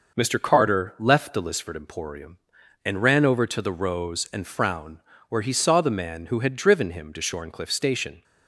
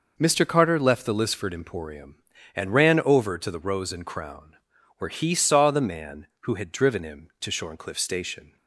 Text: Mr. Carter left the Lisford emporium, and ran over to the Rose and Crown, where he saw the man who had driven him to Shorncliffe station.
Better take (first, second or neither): second